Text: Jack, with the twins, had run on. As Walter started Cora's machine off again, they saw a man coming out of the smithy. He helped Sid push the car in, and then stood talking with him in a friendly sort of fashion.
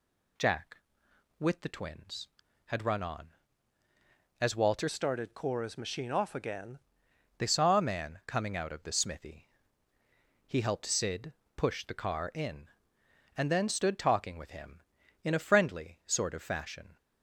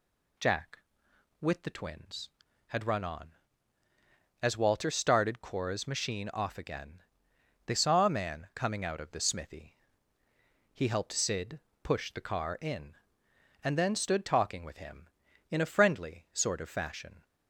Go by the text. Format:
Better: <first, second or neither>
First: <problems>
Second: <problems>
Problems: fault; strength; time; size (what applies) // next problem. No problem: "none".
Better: second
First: changes voice from "started" to "again"; from 4.8 to 6.7 s; 1.9 s long // pauses between "Sid" and "push"; slight; at 11.3 s; 0.24 s long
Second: pauses between "Sid" and "push"; slight; at 11.5 s; 0.24 s long